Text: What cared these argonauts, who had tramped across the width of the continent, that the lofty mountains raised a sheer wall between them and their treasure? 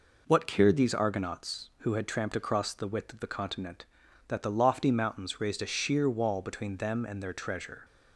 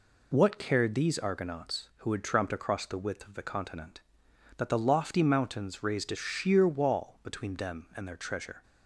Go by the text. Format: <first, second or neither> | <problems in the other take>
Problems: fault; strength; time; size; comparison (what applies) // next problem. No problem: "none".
neither | none